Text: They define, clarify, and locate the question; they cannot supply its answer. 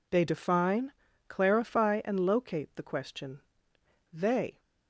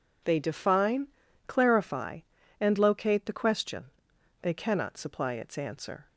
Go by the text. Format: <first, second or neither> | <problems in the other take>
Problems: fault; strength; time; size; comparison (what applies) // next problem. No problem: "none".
second | stops before "cannot supply its answer"; at 4.5 s